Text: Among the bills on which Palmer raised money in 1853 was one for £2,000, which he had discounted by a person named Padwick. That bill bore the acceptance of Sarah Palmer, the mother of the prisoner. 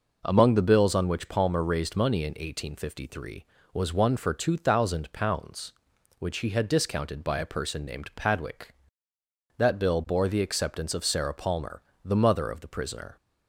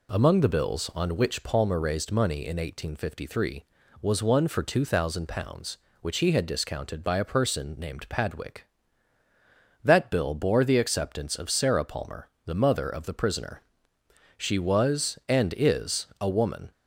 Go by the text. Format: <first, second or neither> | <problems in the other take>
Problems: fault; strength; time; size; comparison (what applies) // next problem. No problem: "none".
first | goes on to say "She was and is a woman"; strong; from 14.3 s on; 2.3 s long